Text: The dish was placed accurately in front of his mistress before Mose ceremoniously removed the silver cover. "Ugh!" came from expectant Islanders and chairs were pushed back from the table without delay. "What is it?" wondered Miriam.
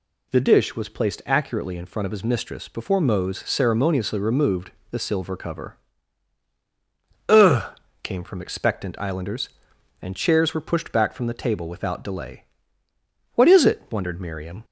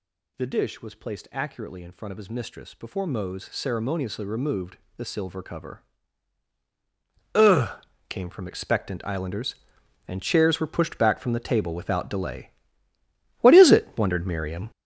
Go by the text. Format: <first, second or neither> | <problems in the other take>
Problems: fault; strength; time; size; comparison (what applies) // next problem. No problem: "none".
first | gets louder; strong; throughout; 9 dB // pauses between "removed" and "the"; slight; at 4.7 s; 0.20 s long; slight in the first